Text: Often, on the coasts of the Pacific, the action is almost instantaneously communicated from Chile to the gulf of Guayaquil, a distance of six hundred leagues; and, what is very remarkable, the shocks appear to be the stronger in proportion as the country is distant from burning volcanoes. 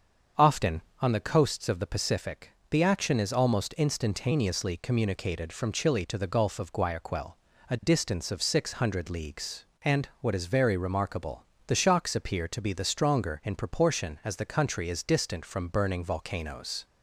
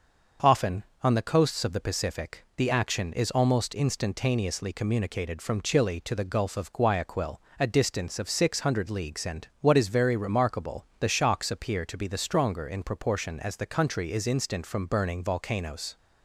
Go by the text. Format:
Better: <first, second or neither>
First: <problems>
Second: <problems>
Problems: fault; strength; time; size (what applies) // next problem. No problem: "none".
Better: first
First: starts louder than the rest; until 1.5 s; 7 dB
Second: starts louder than the rest; until 1.6 s; 6.5 dB // says "instant" for "distant"; at 14.2 s